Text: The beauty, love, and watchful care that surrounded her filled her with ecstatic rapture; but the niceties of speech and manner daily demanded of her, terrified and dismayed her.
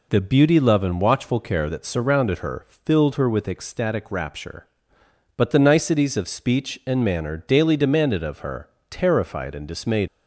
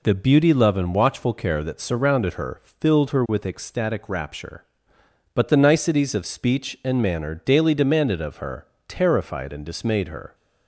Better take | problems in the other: second | stops before "her"; at 10.0 s

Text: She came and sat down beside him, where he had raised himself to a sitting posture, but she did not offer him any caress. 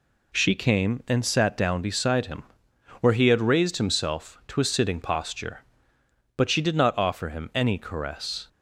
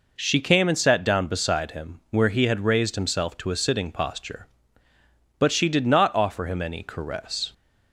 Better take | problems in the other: neither | none

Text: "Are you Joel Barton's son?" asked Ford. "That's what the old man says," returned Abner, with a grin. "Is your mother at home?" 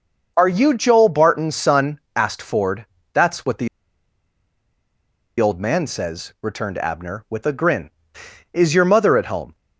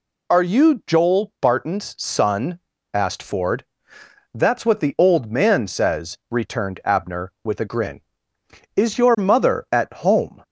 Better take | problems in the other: second | starts louder than the rest; noticeable; until 1.3 s; 6 dB // pauses between "the" and "old"; strong; at 3.6 s; 1.7 s long

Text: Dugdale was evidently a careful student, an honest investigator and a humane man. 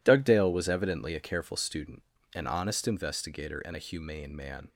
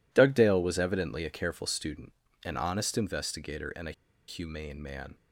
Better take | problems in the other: first | pauses between "a" and "humane"; at 3.9 s; 0.36 s long

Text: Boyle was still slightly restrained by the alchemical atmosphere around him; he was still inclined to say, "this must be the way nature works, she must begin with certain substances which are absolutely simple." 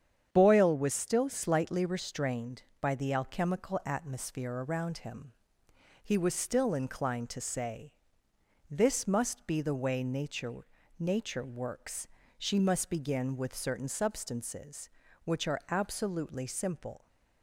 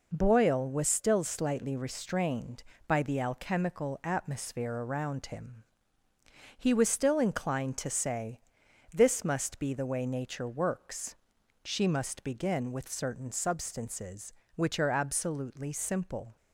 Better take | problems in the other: second | starts louder than the rest; strong; until 1.3 s; 8.5 dB // says "nature" twice; at 11.0 s

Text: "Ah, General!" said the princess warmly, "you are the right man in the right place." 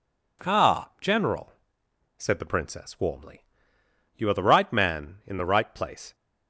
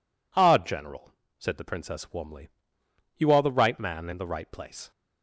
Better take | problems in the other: neither | none

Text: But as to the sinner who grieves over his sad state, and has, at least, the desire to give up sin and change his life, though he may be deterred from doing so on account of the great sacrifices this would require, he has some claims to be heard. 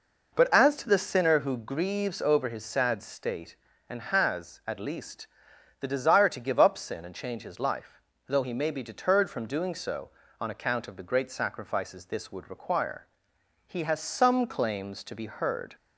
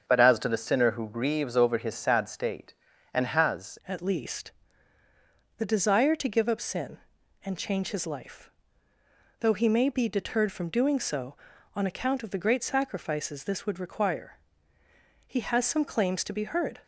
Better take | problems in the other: first | starts louder than the rest; until 1.0 s; 7 dB // changes voice at "at"; from 3.8 s on; 12.9 s long

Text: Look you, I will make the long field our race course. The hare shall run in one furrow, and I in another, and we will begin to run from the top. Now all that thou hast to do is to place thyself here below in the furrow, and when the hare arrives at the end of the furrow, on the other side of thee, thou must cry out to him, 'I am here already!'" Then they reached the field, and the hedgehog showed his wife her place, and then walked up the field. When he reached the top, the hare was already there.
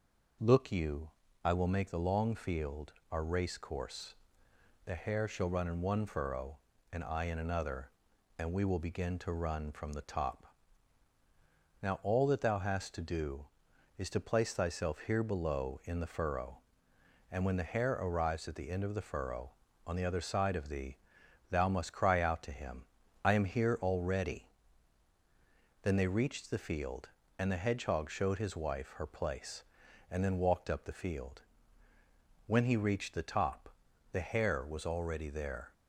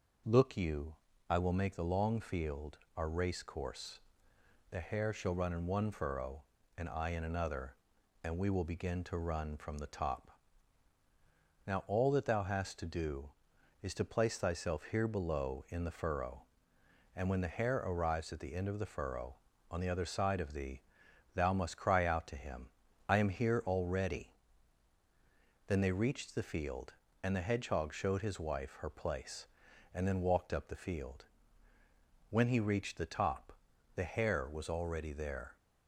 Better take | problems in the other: neither | pauses between "field" and "our"; slight; the same in both

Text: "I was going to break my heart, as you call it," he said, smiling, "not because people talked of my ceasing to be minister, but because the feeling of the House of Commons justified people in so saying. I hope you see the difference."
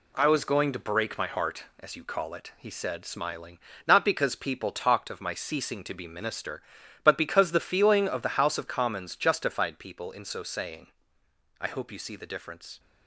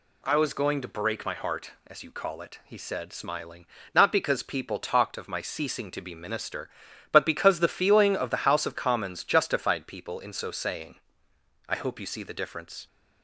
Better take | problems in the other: second | gets quieter; noticeable; throughout; 6 dB

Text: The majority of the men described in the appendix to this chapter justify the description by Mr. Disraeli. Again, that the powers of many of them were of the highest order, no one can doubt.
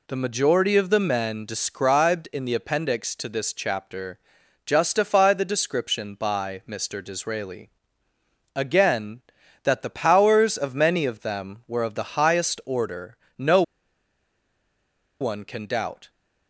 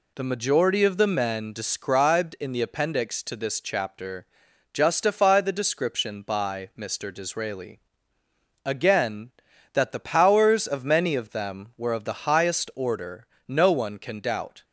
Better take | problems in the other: second | pauses between "chapter" and "justify"; noticeable; at 4.1 s; 0.48 s long; noticeable in the second // pauses between "no" and "one"; strong; at 13.6 s; 1.5 s long

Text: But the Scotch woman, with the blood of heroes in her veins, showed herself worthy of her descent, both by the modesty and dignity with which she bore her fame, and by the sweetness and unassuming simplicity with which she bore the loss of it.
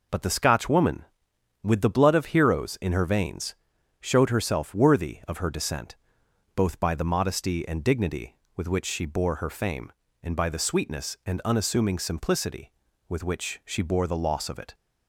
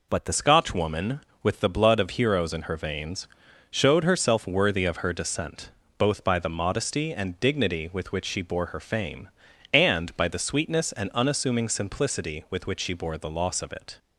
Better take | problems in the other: first | changes voice at "Scotch"; from 0.3 s on; 13.6 s long

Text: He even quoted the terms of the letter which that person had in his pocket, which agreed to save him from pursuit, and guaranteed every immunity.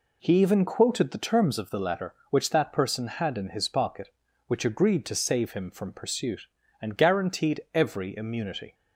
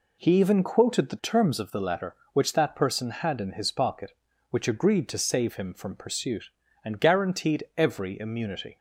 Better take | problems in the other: neither | none

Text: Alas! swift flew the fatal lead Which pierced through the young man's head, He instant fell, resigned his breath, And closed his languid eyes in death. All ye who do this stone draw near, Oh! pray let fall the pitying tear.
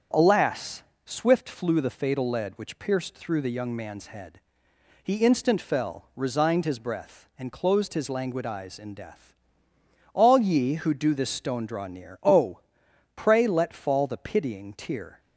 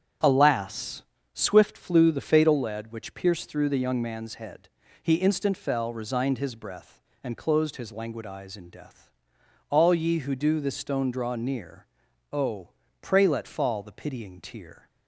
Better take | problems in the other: neither | starts louder than the rest; strong; the same in both

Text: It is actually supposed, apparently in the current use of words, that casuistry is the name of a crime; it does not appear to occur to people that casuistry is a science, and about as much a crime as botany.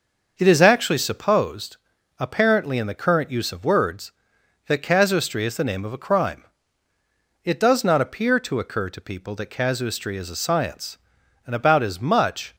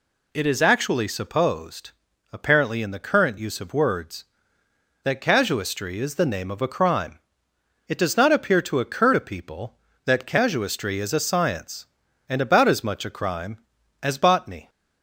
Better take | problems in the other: second | starts louder than the rest; noticeable; until 1.3 s; 6 dB // stops before "a crime as botany"; at 12.5 s

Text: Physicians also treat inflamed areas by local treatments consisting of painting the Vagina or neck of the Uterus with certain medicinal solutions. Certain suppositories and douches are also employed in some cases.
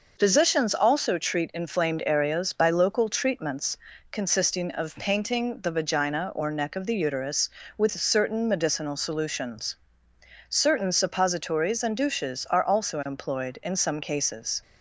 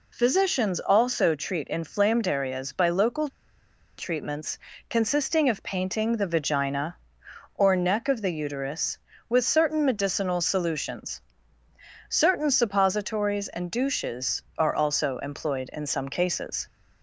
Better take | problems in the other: first | pauses between "local" and "treatments"; noticeable; at 3.2 s; 0.69 s long // pauses between "treatments" and "consisting"; slight; at 4.5 s; 0.32 s long; slight in the first

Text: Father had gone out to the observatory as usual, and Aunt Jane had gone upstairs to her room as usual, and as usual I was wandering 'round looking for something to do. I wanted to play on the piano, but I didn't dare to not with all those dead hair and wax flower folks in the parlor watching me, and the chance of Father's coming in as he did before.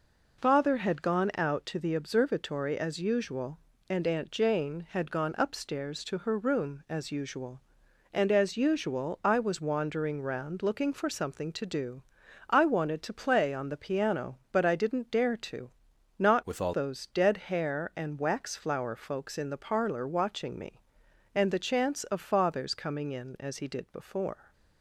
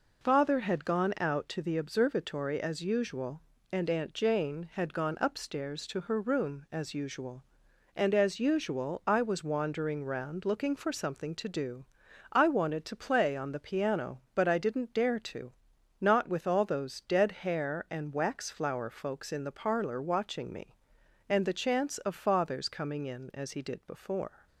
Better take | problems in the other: second | pauses between "to" and "not"; noticeable; at 15.7 s; 0.50 s long; noticeable in the second // changes voice from "with" to "all"; from 16.4 to 16.7 s; 0.3 s long

